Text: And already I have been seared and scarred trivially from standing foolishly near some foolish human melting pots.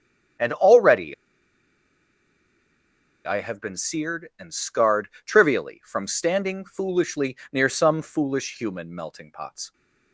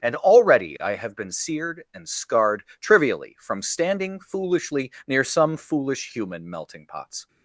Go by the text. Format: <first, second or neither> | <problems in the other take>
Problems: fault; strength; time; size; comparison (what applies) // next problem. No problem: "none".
second | starts louder than the rest; strong; until 3.5 s; 8.5 dB; strong in the second // pauses between "already" and "I"; strong; at 1.1 s; 2.1 s long // pauses between "scarred" and "trivially"; slight; at 5.0 s; 0.16 s long; slight in the second // pauses between "foolishly" and "near"; slight; at 7.3 s; 0.16 s long; slight in the second